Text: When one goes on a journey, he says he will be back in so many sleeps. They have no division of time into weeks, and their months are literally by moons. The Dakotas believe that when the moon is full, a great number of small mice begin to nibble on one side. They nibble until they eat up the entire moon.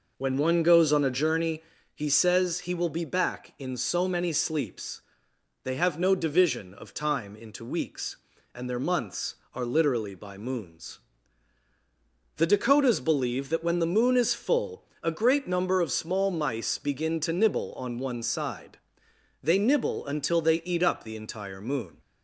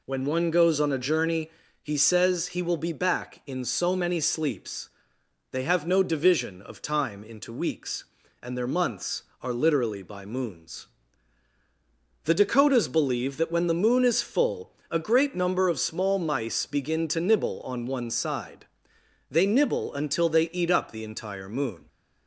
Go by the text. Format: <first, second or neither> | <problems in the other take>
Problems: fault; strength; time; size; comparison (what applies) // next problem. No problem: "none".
second | starts louder than the rest; noticeable; until 1.3 s; 5 dB